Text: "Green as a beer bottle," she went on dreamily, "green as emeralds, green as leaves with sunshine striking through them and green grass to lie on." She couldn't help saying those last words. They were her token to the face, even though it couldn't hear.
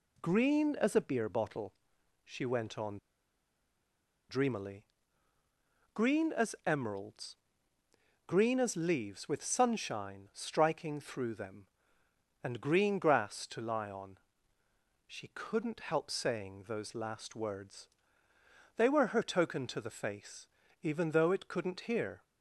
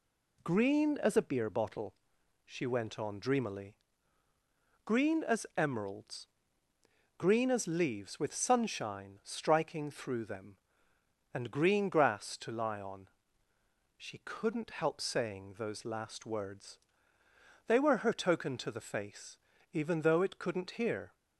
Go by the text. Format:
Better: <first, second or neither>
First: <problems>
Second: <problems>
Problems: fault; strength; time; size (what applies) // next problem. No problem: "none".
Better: second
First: pauses between "on" and "dreamily"; strong; at 2.9 s; 1.3 s long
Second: none